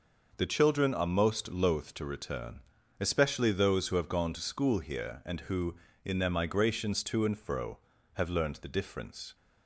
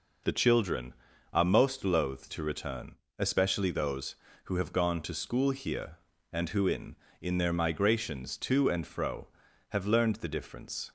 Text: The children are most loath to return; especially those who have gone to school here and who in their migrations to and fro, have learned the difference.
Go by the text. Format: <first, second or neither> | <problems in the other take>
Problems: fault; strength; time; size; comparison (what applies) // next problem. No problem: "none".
first | says "in" twice; at 7.2 s